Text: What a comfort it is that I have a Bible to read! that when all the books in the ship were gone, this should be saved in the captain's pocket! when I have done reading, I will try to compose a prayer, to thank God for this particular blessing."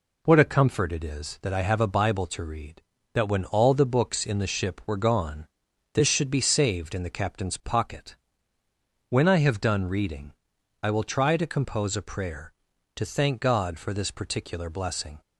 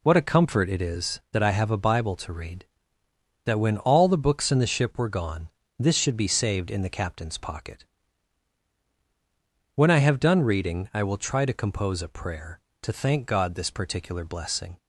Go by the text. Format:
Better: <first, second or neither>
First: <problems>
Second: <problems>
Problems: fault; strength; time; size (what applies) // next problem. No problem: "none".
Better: first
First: none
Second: skips "for"; at 13.5 s